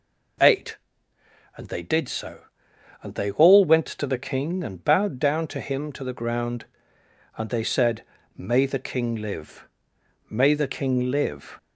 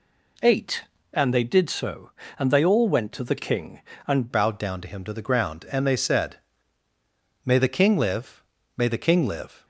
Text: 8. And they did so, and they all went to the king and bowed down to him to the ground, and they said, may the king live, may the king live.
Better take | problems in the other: first | changes voice at "bowed"; from 4.3 s on; 5.3 s long

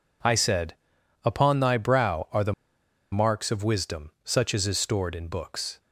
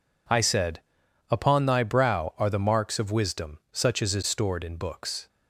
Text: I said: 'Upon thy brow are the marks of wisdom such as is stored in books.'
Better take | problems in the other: second | pauses between "the" and "marks"; noticeable; at 2.5 s; 0.58 s long

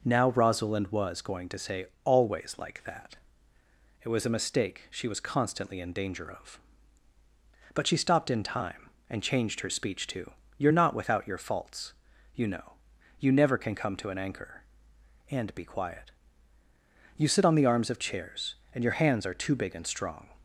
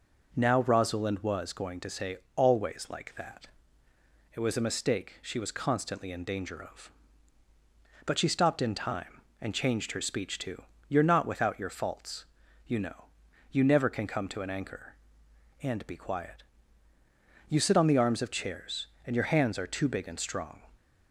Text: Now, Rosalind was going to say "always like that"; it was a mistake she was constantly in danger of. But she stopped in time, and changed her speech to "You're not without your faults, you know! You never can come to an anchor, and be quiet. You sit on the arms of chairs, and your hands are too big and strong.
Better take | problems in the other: neither | pauses between "say" and "always"; slight; the same in both // pauses between "to" and "You're"; slight; the same in both

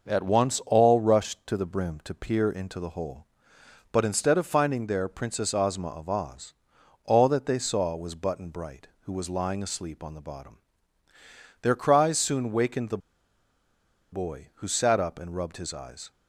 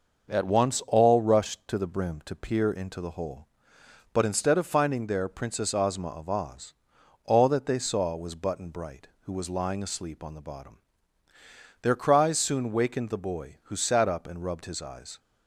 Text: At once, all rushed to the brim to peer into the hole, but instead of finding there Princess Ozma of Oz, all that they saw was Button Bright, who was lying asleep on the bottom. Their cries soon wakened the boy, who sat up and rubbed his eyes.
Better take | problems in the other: second | pauses between "the" and "boy"; at 12.9 s; 1.1 s long

